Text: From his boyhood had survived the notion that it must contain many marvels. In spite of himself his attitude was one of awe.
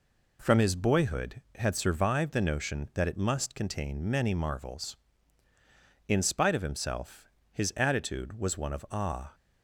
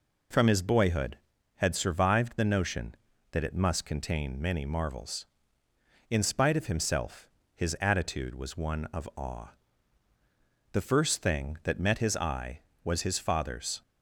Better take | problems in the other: first | pauses between "himself" and "his"; slight; at 7.2 s; 0.26 s long; slight in the first // goes on to say "The first thing that met his eye was his father's"; strong; from 10.7 s on; 3.1 s long

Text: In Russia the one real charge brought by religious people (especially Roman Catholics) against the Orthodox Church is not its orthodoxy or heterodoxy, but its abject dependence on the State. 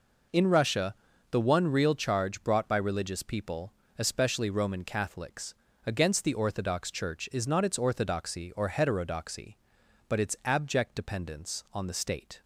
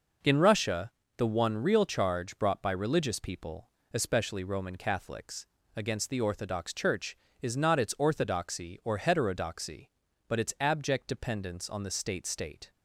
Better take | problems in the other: first | pauses between "Russia" and "the"; slight; at 0.9 s; 0.26 s long; slight in the first // says "State" twice; at 12.2 s

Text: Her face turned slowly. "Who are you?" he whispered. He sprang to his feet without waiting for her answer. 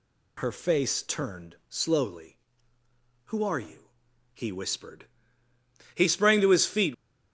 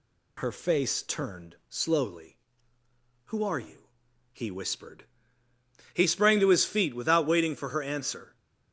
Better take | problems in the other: second | stops before "without waiting for her answer"; at 6.9 s

